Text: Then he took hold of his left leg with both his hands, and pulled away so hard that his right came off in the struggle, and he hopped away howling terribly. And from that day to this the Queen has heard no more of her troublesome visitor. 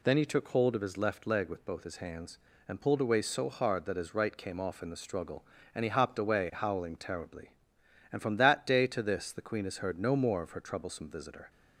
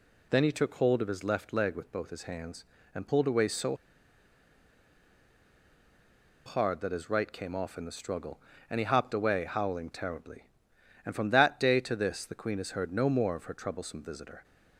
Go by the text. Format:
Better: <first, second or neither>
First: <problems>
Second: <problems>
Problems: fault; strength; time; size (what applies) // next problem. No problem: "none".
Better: first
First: none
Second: pauses between "so" and "hard"; strong; at 3.7 s; 2.6 s long